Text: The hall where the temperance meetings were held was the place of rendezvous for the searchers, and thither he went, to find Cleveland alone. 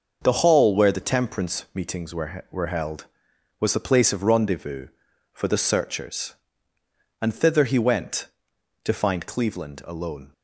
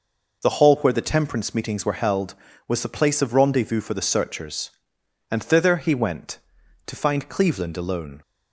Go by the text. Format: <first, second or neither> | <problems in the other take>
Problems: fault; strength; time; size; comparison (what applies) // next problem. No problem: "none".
second | says "were" twice; at 2.5 s